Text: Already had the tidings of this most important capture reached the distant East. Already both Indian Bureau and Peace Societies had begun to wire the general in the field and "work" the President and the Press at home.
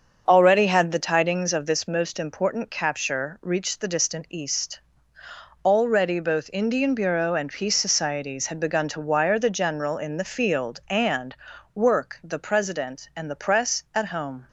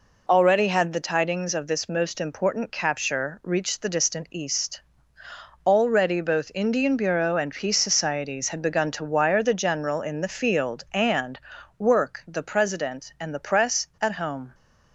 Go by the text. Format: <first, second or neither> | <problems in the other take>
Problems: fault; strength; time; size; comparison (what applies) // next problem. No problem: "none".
second | starts louder than the rest; until 2.1 s; 6.5 dB // pauses between "and" and "work"; at 11.3 s; 0.38 s long; also in the second